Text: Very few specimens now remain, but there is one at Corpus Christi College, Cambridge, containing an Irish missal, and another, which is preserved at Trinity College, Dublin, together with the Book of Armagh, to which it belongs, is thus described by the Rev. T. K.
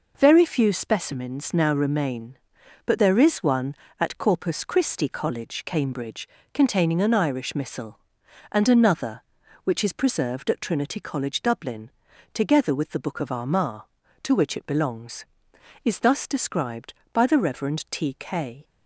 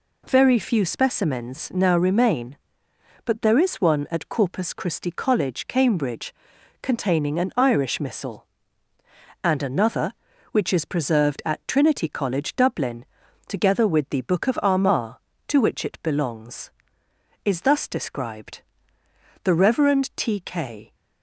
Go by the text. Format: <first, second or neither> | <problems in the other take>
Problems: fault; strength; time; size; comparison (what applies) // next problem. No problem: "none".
first | skips "by"; at 19.0 s